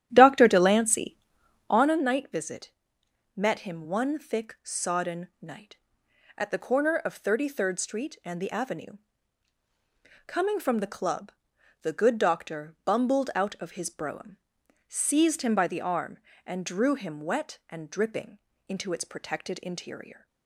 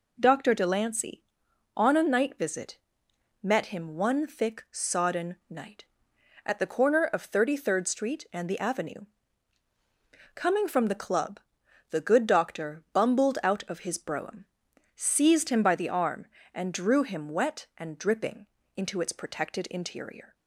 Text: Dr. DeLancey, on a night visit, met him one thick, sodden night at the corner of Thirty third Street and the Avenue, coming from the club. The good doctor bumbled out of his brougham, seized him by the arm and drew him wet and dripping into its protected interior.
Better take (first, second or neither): second